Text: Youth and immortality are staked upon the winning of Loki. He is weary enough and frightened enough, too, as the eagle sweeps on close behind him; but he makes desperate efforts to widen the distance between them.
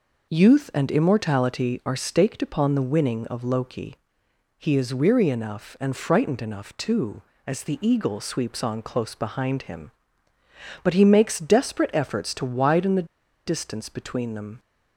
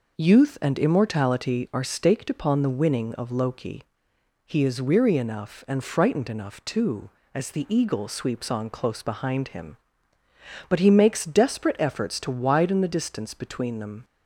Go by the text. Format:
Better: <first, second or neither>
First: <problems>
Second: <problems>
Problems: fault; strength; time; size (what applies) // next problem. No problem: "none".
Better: second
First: pauses between "the" and "distance"; at 13.0 s; 0.39 s long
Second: none